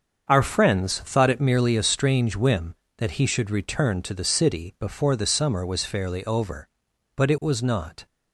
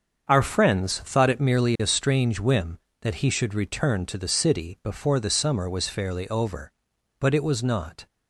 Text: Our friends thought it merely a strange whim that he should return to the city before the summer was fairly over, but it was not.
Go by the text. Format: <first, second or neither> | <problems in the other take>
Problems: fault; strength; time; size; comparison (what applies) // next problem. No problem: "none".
neither | starts louder than the rest; the same in both